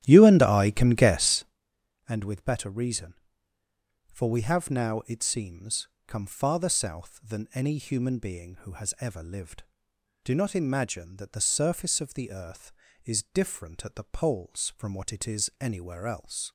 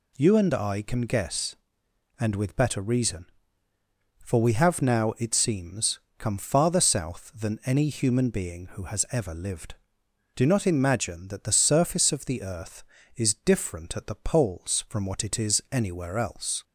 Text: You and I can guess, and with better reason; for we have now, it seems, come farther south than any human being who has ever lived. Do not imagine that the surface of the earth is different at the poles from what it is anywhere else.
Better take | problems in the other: second | starts louder than the rest; strong; until 1.6 s; 12.5 dB

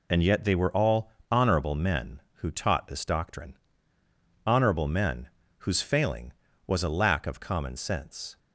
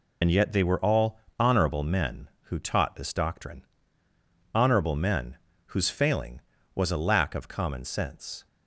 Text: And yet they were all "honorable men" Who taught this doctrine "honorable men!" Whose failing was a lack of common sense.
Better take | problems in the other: first | loses the start of "And"; at 0.2 s; 35 ms // pauses between "all" and "honorable"; slight; at 1.2 s; 0.18 s long; slight in the first // pauses between "doctrine" and "honorable"; noticeable; at 3.6 s; 0.88 s long; noticeable in the first

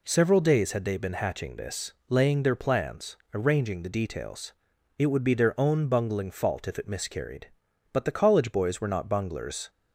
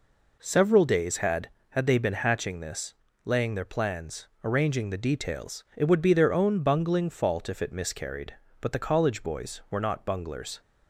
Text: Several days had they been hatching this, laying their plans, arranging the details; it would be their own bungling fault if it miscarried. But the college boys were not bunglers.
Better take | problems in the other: first | says "had" twice; at 1.6 s

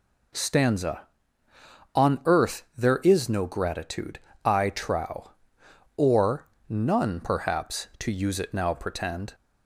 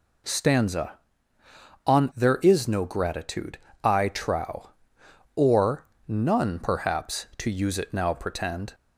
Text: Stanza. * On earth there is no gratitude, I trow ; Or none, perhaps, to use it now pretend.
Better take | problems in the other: first | skips "earth"; at 2.1 s // pauses between "Or" and "none"; slight; at 5.8 s; 0.20 s long; slight in the first

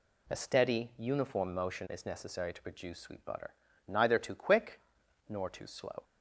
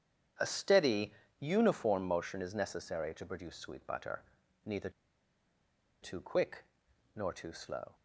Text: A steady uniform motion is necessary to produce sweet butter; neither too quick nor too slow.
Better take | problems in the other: first | starts louder than the rest; strong; until 1.6 s; 8.5 dB // pauses between "steady" and "uniform"; slight; at 1.1 s; 0.26 s long // pauses between "neither" and "too"; at 4.8 s; 1.1 s long // pauses between "quick" and "nor"; noticeable; at 6.6 s; 0.50 s long; noticeable in the first

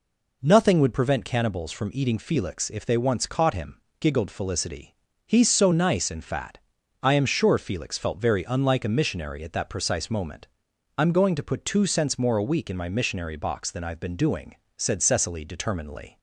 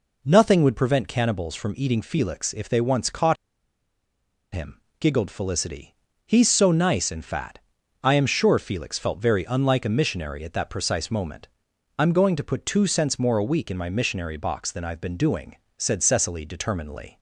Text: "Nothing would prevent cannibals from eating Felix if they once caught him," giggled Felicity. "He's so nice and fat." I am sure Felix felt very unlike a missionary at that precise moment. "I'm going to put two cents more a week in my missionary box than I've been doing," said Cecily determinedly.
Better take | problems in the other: first | pauses between "caught" and "him"; at 3.3 s; 1.1 s long

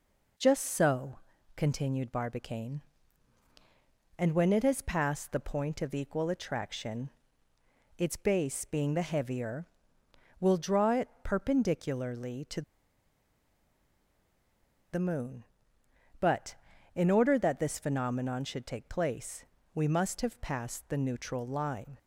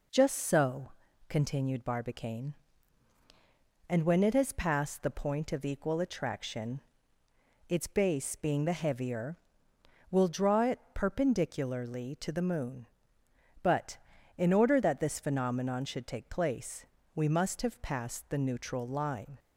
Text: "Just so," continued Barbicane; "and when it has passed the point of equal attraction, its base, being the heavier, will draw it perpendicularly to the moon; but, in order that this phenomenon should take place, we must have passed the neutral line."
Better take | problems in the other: second | pauses between "to" and "the"; strong; at 12.6 s; 2.3 s long

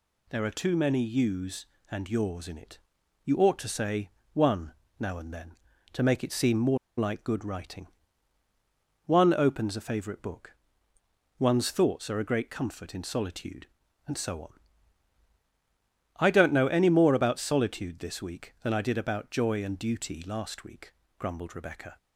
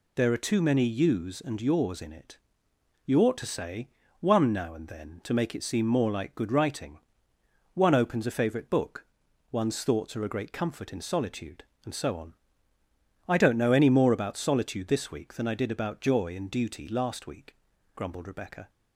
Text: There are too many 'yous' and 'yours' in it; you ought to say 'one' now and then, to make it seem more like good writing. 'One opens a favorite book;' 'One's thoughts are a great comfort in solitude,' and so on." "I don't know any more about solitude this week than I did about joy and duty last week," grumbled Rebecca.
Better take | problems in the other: second | pauses between "say" and "one"; slight; at 4.0 s; 0.24 s long; slight in the second // pauses between "one" and "now"; slight; at 4.7 s; 0.26 s long // pauses between "more" and "like"; slight; at 6.7 s; 0.21 s long

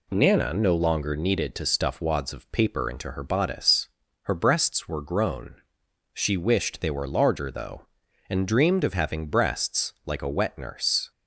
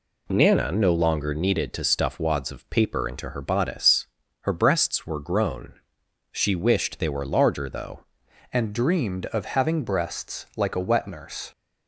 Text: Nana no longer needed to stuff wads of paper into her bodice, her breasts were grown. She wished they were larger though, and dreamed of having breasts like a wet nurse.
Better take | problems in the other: first | changes voice at "and"; from 8.5 s on; 3.0 s long

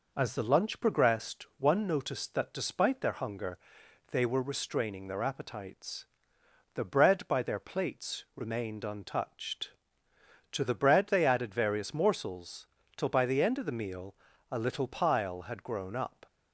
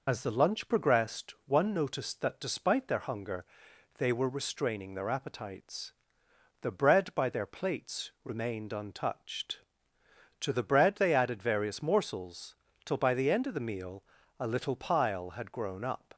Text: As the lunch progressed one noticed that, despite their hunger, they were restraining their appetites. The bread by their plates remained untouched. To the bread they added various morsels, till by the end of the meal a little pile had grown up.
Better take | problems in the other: first | loses the start of "As"; at 0.0 s; 40 ms // pauses between "meal" and "a"; slight; at 14.0 s; 0.36 s long; slight in the first

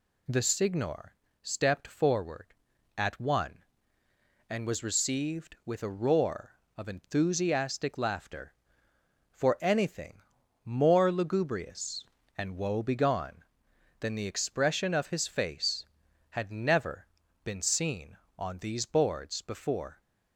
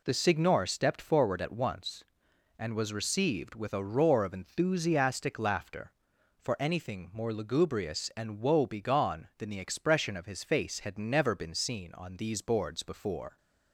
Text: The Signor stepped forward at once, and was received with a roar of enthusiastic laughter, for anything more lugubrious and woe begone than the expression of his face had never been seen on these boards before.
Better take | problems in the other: second | pauses between "Signor" and "stepped"; slight; at 1.1 s; 0.30 s long // says "one" for "once"; at 3.1 s // pauses between "anything" and "more"; at 10.2 s; 0.42 s long // pauses between "never" and "been"; at 17.0 s; 0.38 s long

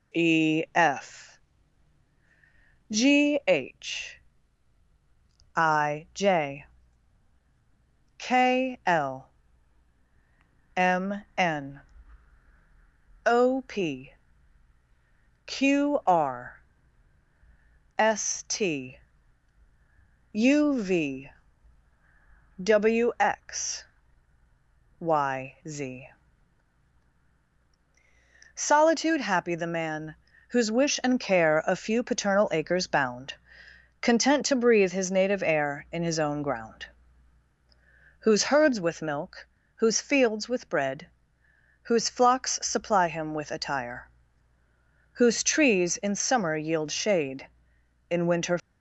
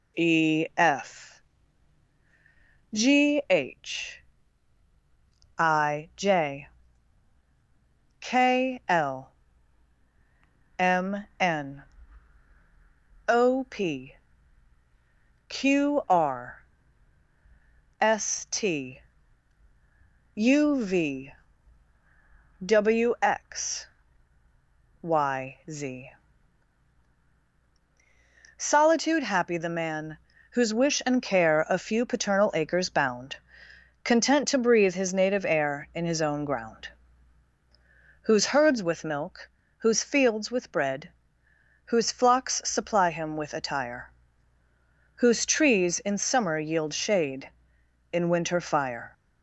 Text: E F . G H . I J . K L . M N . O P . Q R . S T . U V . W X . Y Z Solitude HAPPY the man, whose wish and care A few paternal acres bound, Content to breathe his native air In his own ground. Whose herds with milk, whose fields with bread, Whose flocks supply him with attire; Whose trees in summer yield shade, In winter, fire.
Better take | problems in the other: second | pauses between "Z" and "Solitude"; strong; at 26.0 s; 2.4 s long; strong in the second // stops before "fire"; at 48.5 s

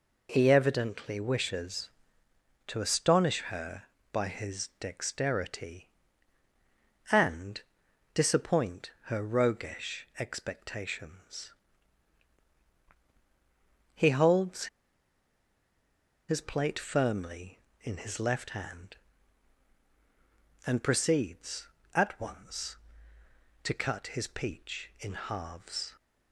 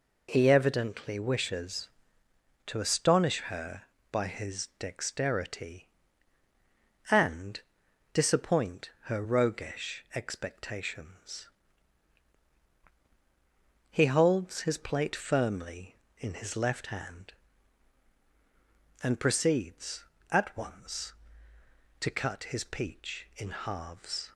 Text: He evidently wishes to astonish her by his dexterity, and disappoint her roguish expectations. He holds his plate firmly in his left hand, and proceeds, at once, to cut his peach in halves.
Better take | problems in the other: second | pauses between "and" and "disappoint"; noticeable; at 7.6 s; 0.54 s long; noticeable in the second // pauses between "holds" and "his"; strong; at 14.6 s; 1.6 s long

